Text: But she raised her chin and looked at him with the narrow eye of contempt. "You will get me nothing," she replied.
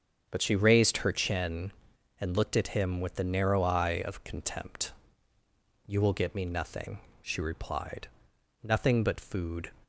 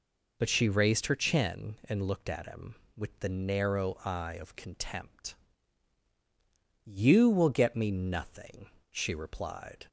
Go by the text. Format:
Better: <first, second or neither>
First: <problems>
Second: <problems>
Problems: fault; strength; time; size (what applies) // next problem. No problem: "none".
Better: second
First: starts louder than the rest; strong; until 1.3 s; 7 dB // goes on to say "Nothing but food"; noticeable; from 8.6 s on; 1.0 s long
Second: none